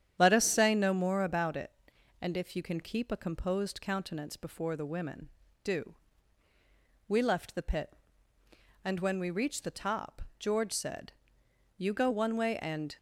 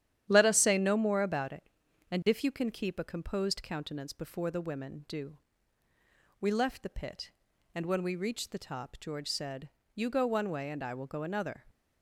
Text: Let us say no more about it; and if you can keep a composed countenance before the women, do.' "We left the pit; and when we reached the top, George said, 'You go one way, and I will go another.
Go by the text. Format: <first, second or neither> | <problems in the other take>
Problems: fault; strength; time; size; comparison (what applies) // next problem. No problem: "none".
second | starts louder than the rest; strong; until 1.1 s; 9.5 dB; strong in the second // stops before "I will go another"; at 12.9 s